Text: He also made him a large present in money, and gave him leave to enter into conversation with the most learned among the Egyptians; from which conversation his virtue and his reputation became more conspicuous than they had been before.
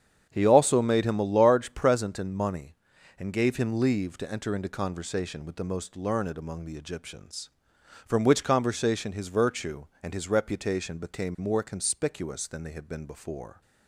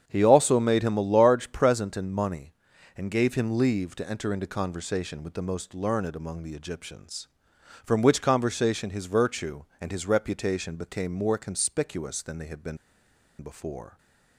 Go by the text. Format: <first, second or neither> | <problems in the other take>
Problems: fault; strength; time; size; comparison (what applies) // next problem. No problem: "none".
first | starts louder than the rest; strong; until 1.0 s; 8 dB; strong in the first // pauses between "been" and "before"; noticeable; at 12.7 s; 0.64 s long